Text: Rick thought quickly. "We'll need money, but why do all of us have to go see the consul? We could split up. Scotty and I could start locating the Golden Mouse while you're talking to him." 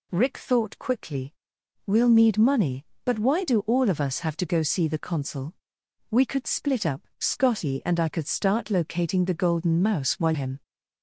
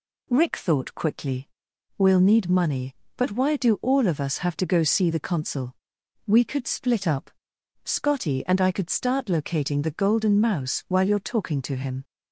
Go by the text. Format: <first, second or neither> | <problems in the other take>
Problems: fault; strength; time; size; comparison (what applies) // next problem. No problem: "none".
second | skips "you're talking to"; at 10.3 s